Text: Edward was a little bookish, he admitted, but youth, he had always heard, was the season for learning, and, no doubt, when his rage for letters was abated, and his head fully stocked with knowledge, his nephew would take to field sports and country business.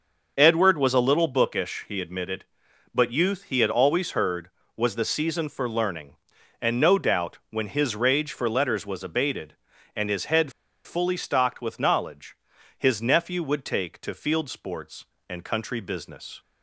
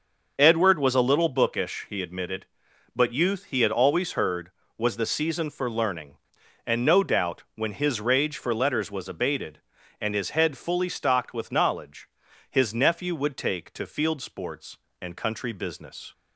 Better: second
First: starts louder than the rest; noticeable; until 1.3 s; 6 dB // pauses between "head" and "fully"; slight; at 10.5 s; 0.33 s long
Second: starts louder than the rest; noticeable; until 1.3 s; 6 dB

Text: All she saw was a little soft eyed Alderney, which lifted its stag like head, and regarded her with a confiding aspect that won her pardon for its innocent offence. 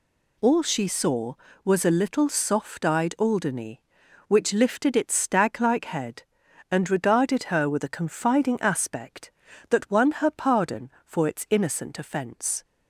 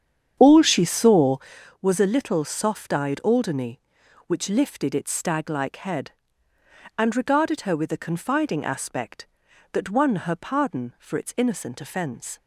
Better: first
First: none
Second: starts louder than the rest; strong; until 1.6 s; 8.5 dB

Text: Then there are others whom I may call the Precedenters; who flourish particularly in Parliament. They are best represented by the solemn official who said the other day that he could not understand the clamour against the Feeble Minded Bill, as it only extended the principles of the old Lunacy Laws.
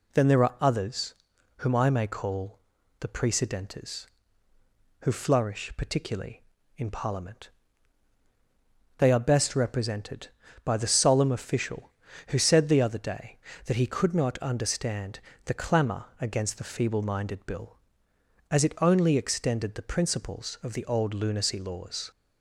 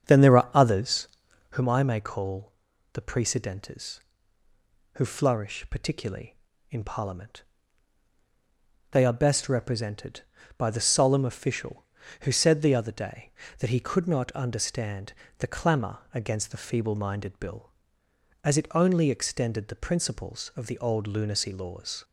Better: first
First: pauses between "others" and "whom"; at 1.1 s; 0.44 s long // pauses between "call" and "the"; at 2.5 s; 0.40 s long // pauses between "understand" and "the"; slight; at 15.2 s; 0.24 s long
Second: starts louder than the rest; strong; until 1.6 s; 7 dB // pauses between "others" and "whom"; at 1.0 s; 0.44 s long // pauses between "call" and "the"; at 2.5 s; 0.40 s long // pauses between "understand" and "the"; slight; at 15.1 s; 0.24 s long

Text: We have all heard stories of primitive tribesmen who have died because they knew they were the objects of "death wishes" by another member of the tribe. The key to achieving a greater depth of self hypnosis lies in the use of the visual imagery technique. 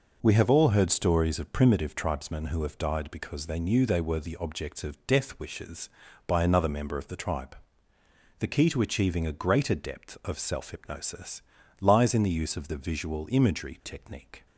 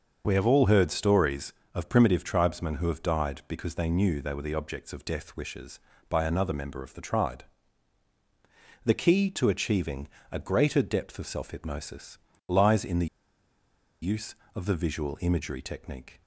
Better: first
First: pauses between "hypnosis" and "lies"; at 11.4 s; 0.38 s long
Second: starts louder than the rest; until 1.2 s; 6.5 dB // pauses between "achieving" and "a"; slight; at 10.0 s; 0.24 s long // pauses between "hypnosis" and "lies"; slight; at 12.1 s; 0.30 s long // pauses between "the" and "use"; noticeable; at 13.0 s; 0.96 s long

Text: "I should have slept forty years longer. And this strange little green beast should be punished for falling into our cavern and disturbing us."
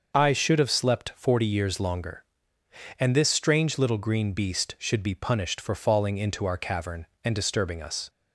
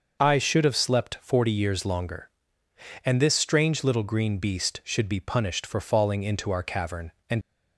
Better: first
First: starts louder than the rest; noticeable; until 1.2 s; 6 dB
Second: starts louder than the rest; noticeable; until 1.2 s; 6 dB // stops before "disturbing us"; at 7.4 s

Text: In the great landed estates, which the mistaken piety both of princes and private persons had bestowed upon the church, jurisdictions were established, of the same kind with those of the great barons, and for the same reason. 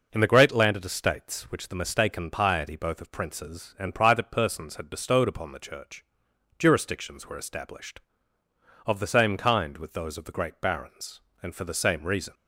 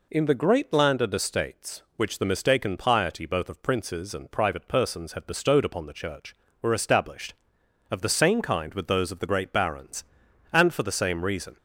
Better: first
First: none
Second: skips "jurisdictions"; at 6.4 s

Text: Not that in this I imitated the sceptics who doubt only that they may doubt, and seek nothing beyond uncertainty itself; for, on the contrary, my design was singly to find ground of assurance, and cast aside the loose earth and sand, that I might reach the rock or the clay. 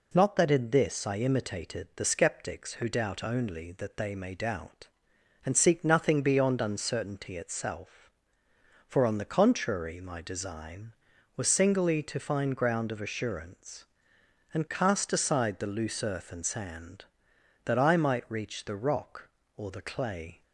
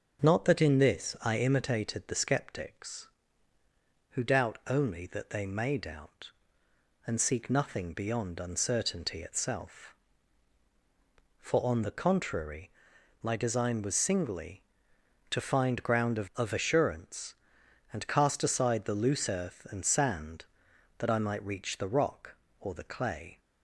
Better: first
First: none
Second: starts louder than the rest; until 1.3 s; 6.5 dB // says "of" twice; at 16.3 s

